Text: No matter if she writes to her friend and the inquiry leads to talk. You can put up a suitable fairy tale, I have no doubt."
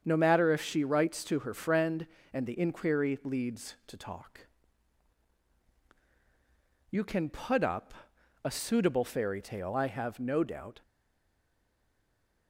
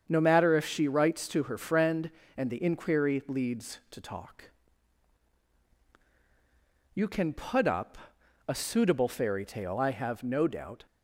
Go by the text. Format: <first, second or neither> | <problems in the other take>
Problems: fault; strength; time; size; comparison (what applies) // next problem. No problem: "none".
second | starts louder than the rest; strong; until 1.0 s; 7.5 dB; strong in the second // pauses between "up" and "a"; noticeable; at 7.9 s; 0.50 s long; noticeable in the second // stays silent after the last word; noticeable; from 10.8 s on; 1.6 s long